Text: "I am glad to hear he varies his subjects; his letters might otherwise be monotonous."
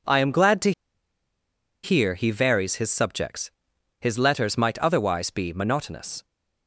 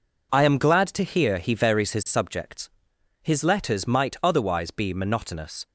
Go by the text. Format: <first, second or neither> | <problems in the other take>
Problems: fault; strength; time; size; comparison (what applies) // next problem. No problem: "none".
second | pauses between "to" and "hear"; at 0.7 s; 1.1 s long